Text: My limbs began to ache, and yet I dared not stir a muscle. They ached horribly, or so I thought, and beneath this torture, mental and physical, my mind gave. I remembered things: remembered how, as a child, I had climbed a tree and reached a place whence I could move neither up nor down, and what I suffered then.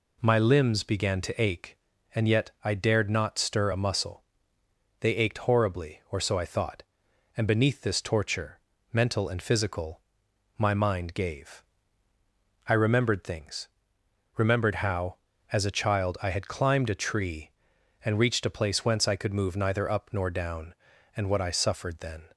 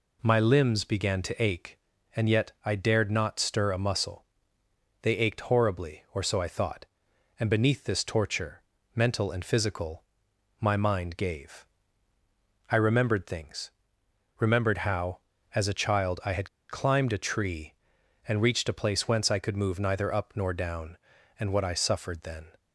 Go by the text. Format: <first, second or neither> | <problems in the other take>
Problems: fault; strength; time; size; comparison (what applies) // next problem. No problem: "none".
first | pauses between "had" and "climbed"; slight; at 16.4 s; 0.20 s long